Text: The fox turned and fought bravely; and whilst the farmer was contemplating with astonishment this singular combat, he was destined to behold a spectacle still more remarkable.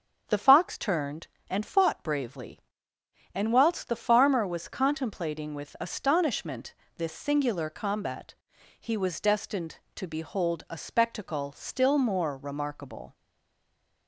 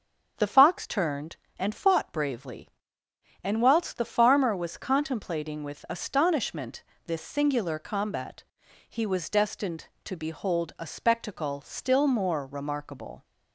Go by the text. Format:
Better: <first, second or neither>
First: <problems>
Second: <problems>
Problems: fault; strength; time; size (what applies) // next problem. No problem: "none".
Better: second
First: starts louder than the rest; until 1.2 s; 7 dB // pauses between "astonishment" and "this"; slight; at 6.7 s; 0.22 s long // stays silent after the last word; slight; from 13.1 s on; 0.9 s long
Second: starts louder than the rest; until 1.3 s; 7 dB // pauses between "astonishment" and "this"; slight; at 6.8 s; 0.22 s long